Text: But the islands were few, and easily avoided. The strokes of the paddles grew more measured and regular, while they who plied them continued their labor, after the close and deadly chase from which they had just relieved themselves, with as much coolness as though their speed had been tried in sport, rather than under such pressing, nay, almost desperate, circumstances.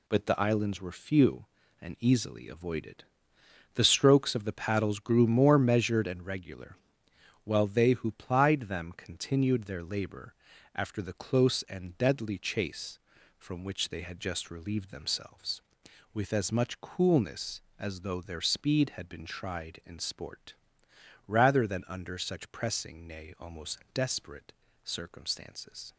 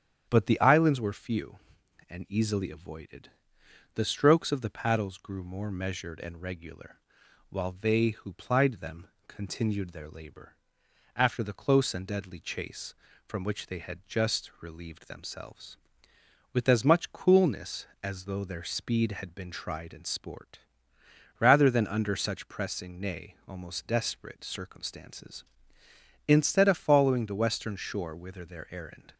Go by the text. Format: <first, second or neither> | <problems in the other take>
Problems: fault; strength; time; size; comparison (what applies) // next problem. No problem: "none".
first | starts louder than the rest; strong; until 1.3 s; 9 dB // pauses between "them" and "continued"; slight; at 9.0 s; 0.19 s long // goes on to say "Instead of following the western shore whither their errand"; strong; from 26.2 s on; 2.8 s long